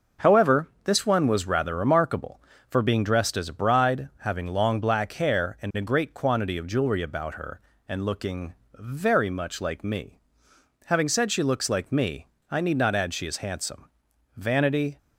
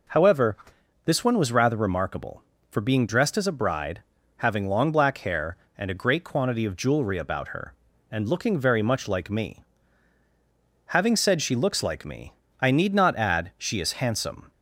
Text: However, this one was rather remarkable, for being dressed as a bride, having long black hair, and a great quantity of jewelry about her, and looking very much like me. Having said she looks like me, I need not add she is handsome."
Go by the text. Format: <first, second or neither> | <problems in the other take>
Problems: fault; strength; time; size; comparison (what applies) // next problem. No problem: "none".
second | pauses between "looking" and "very"; slight; at 8.5 s; 0.20 s long // goes on to say "Vanity"; from 14.3 s on; 0.60 s long